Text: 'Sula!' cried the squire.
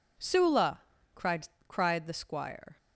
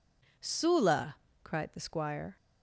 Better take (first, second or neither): second